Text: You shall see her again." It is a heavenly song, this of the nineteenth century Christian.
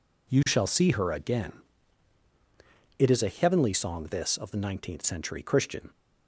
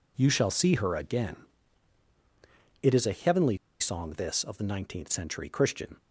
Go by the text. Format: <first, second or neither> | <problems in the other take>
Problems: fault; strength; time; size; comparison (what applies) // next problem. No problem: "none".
first | pauses between "heavenly" and "song"; slight; at 3.5 s; 0.22 s long